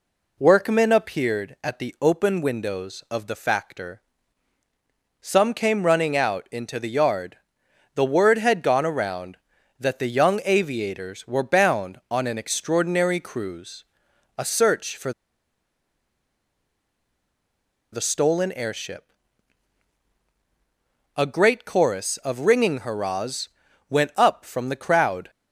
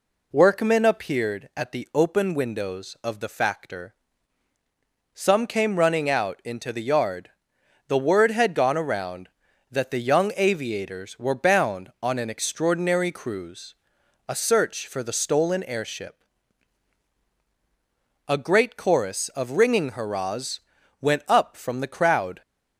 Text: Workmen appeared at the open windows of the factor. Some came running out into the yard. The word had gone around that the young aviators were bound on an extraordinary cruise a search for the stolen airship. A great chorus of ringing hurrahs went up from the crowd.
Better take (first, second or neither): second